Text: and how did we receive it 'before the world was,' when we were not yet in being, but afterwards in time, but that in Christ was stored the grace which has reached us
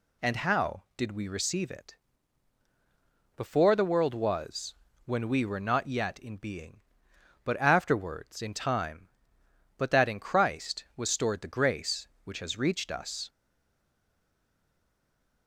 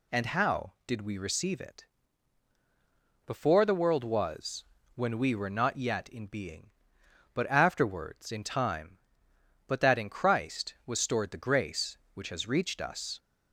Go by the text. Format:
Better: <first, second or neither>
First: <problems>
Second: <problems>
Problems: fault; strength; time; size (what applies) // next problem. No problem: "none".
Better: second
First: pauses between "it" and "before"; strong; at 1.9 s; 1.4 s long // stays silent after the last word; from 13.2 s on; 2.2 s long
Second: pauses between "it" and "before"; strong; at 1.8 s; 1.4 s long